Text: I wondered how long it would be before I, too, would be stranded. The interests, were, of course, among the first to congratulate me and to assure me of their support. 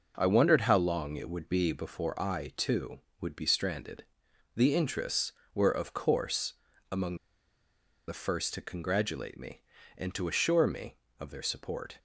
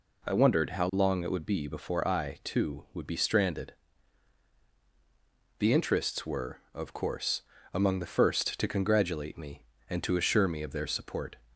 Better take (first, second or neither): second